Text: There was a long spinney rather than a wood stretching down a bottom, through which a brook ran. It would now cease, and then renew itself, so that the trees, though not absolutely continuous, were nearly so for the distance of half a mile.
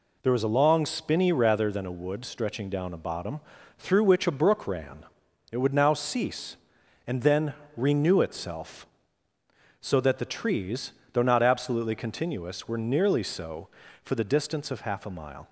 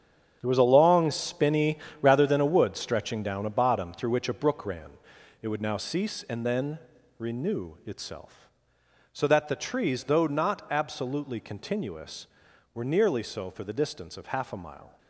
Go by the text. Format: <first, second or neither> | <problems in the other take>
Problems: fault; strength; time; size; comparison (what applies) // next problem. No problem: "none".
first | gets quieter; strong; throughout; 11.5 dB // pauses between "spinney" and "rather"; slight; at 1.7 s; 0.22 s long // pauses between "then" and "renew"; at 6.7 s; 0.40 s long; slight in the first